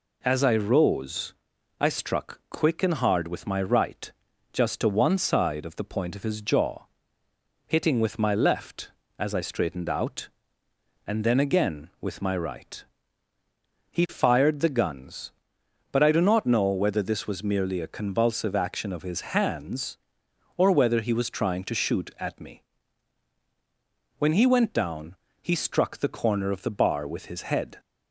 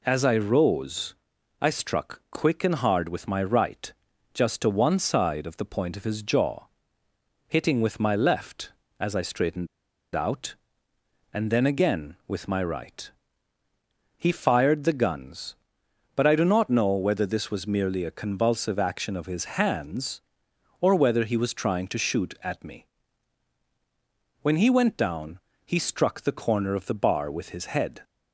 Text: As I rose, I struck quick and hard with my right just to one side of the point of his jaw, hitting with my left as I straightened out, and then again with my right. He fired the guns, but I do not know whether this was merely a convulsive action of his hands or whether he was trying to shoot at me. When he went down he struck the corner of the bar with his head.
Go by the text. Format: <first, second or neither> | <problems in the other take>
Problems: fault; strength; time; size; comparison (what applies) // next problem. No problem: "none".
first | pauses between "right" and "just"; at 3.9 s; 0.42 s long; also in the first // pauses between "straightened" and "out"; noticeable; at 9.6 s; 0.48 s long // pauses between "down" and "he"; slight; at 25.3 s; 0.26 s long; slight in the first